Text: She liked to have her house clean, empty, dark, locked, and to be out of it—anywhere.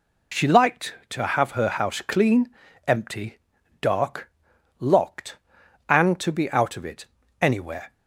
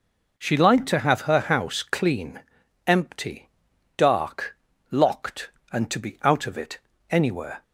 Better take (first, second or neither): neither